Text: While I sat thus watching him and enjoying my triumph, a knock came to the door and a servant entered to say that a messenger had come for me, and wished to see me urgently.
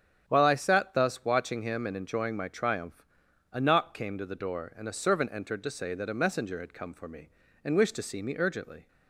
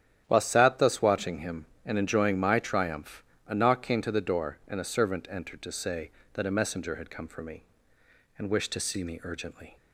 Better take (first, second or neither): first